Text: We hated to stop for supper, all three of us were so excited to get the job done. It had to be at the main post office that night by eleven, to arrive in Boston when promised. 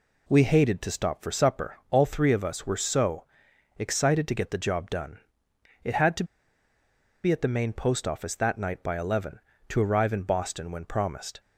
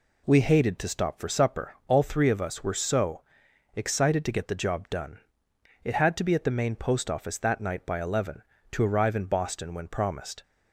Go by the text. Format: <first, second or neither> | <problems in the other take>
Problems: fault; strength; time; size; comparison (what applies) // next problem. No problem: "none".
second | pauses between "so" and "excited"; noticeable; at 3.2 s; 0.56 s long; noticeable in the second // pauses between "to" and "be"; at 6.2 s; 0.99 s long